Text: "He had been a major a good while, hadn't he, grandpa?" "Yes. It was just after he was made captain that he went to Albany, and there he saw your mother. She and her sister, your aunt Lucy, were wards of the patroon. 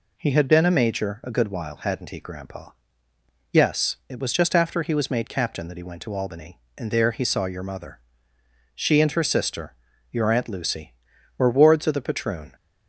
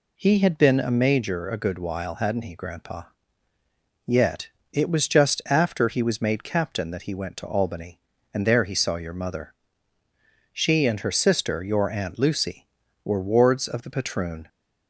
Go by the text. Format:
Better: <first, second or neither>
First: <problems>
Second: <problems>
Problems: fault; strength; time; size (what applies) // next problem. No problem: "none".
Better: first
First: none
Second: says "Yet" for "Yes"; at 4.0 s